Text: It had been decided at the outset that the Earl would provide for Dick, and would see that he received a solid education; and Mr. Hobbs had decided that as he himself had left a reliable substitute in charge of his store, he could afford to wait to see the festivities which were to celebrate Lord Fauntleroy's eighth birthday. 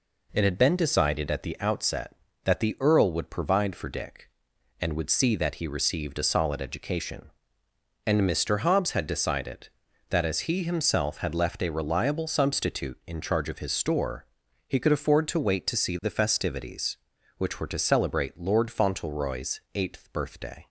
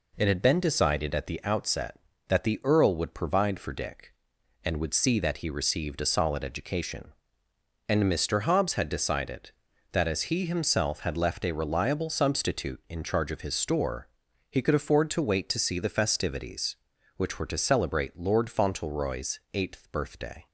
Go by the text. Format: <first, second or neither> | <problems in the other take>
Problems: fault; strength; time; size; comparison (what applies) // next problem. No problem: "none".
neither | pauses between "Fauntleroy's" and "eighth"; slight; the same in both